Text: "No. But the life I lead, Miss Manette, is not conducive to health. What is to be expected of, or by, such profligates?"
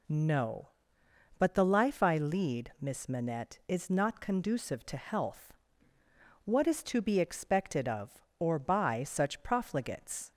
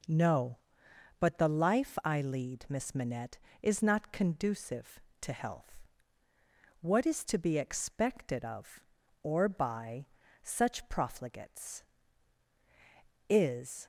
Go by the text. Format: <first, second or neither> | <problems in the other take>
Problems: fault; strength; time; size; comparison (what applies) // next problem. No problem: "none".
first | goes on to say "Is"; from 13.2 s on; 0.56 s long